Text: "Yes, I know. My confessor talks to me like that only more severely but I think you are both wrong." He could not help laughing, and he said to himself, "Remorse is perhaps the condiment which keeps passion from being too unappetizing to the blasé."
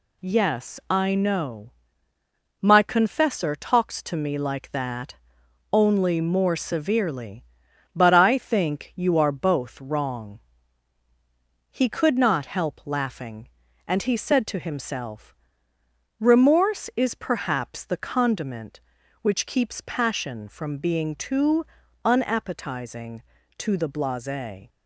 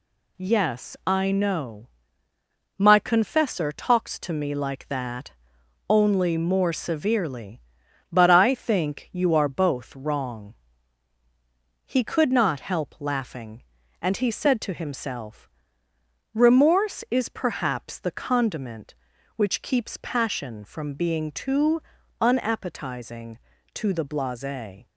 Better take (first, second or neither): neither